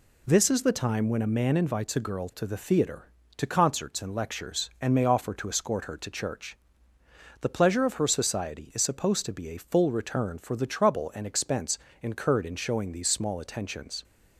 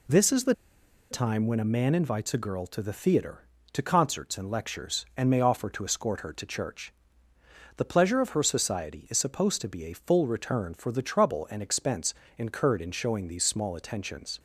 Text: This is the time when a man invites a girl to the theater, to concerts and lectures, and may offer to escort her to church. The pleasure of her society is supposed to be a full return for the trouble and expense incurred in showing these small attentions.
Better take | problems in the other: first | pauses between "the" and "time"; noticeable; at 0.5 s; 0.57 s long // pauses between "expense" and "incurred"; slight; at 12.1 s; 0.24 s long; slight in the first

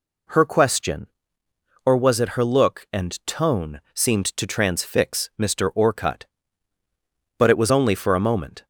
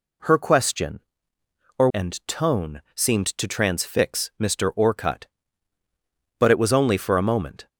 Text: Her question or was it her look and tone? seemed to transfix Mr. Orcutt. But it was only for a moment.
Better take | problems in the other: first | skips "was it her look"; at 1.8 s

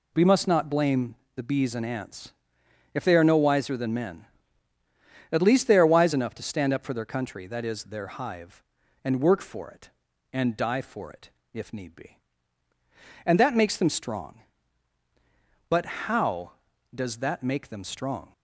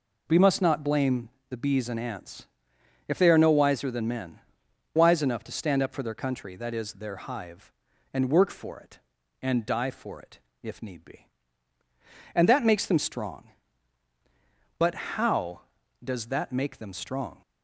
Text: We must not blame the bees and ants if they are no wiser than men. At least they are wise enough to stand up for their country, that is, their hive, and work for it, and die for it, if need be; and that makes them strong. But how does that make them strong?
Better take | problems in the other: first | pauses between "blame" and "the"; slight; at 1.2 s; 0.22 s long; slight in the first // pauses between "ants" and "if"; noticeable; at 2.4 s; 0.60 s long; noticeable in the first // skips "At least they are"; at 4.6 s

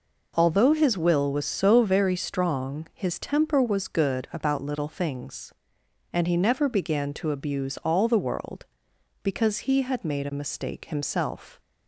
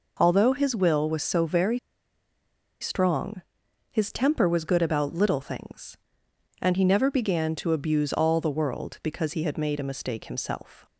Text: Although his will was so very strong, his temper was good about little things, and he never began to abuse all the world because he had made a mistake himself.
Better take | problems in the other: first | pauses between "very" and "strong"; at 1.7 s; 1.0 s long

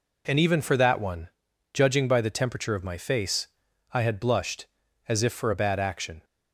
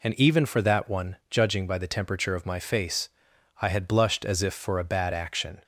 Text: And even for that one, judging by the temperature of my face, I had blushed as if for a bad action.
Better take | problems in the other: neither | none

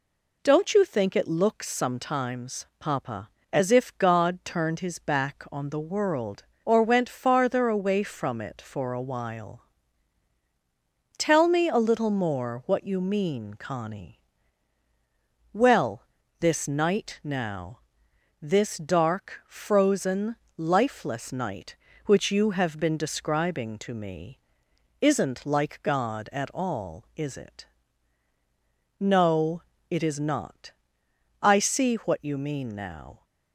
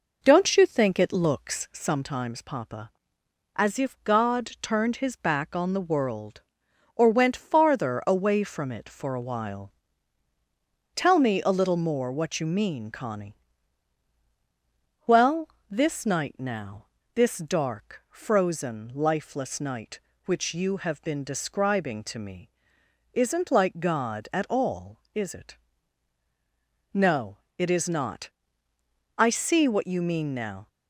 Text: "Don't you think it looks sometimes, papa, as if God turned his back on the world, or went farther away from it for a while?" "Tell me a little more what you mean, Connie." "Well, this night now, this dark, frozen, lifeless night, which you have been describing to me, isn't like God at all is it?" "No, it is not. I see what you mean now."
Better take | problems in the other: first | starts louder than the rest; noticeable; until 1.9 s; 4.5 dB

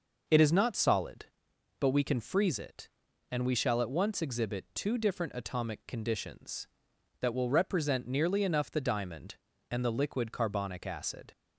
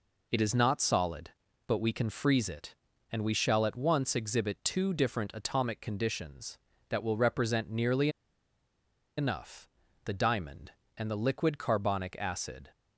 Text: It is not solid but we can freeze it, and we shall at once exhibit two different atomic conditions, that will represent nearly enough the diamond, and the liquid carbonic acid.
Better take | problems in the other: first | pauses between "nearly" and "enough"; at 8.0 s; 1.0 s long // pauses between "enough" and "the"; slight; at 9.6 s; 0.36 s long

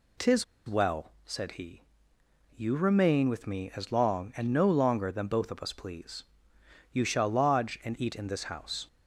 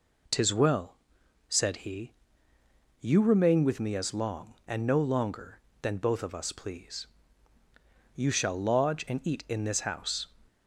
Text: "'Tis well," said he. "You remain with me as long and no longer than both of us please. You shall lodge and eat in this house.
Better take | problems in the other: second | pauses between "Tis" and "well"; slight; at 0.4 s; 0.24 s long

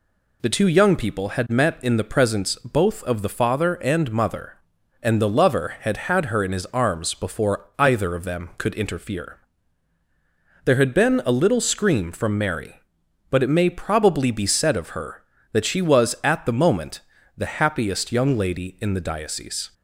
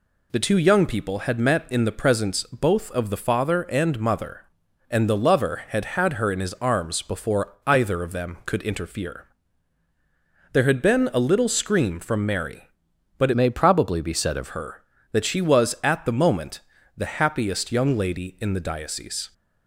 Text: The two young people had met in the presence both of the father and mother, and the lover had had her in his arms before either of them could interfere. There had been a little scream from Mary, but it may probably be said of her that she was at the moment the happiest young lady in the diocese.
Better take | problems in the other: first | changes voice from "may" to "of"; from 13.3 to 14.4 s; 1.1 s long // pauses between "moment" and "the"; slight; at 16.6 s; 0.36 s long; slight in the first

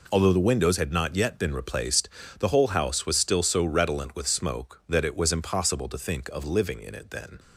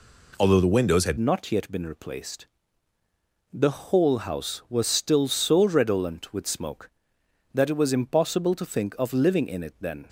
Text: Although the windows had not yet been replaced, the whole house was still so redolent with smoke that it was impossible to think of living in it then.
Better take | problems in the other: first | changes voice at "not"; from 1.1 s on; 8.9 s long

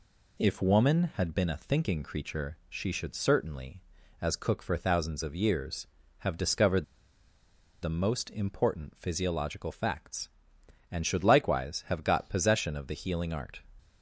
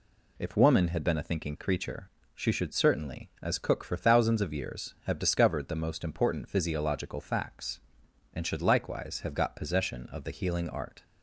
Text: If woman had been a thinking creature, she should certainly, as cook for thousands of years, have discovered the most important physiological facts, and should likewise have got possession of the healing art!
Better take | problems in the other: second | pauses between "discovered" and "the"; noticeable; at 6.8 s; 0.97 s long

